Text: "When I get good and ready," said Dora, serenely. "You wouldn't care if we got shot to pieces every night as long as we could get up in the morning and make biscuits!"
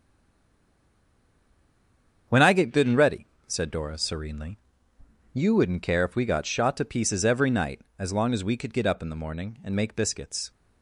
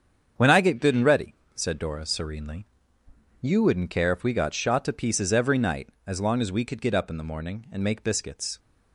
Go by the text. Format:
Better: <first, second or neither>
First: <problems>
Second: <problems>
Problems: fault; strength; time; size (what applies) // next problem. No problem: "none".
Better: second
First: stays silent before the first word; until 2.2 s; 2.2 s long // starts louder than the rest; strong; until 3.5 s; 7.5 dB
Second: starts louder than the rest; strong; until 1.5 s; 7.5 dB